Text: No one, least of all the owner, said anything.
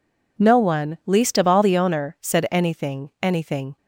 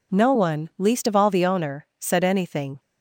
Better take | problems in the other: second | says "anything" twice; at 3.2 s

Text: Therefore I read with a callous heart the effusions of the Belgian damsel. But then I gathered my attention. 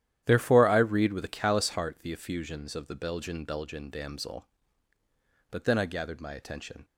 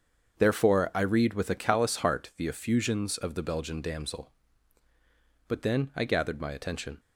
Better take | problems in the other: second | starts louder than the rest; strong; until 1.2 s; 11 dB; also in the second // says "Belgian" twice; at 3.4 s

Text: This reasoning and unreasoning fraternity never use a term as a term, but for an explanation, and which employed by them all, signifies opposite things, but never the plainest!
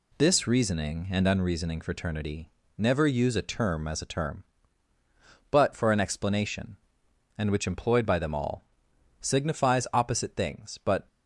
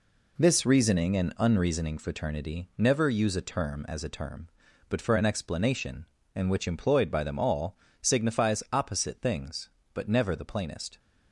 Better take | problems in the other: second | pauses between "fraternity" and "never"; slight; at 2.4 s; 0.28 s long // stops before "never the plainest"; at 11.0 s

